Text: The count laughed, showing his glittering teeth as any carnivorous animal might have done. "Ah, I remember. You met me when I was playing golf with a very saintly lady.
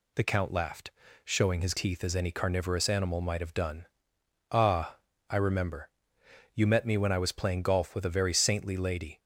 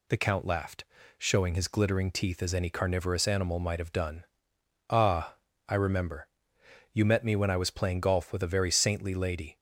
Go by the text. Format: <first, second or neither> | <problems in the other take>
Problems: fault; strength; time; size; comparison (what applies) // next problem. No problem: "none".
second | skips "glittering"; at 1.7 s